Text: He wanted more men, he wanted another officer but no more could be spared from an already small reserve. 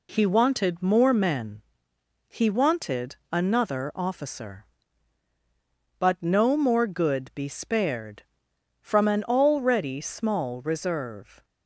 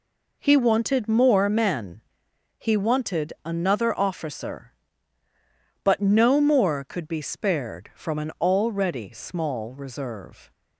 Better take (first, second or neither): second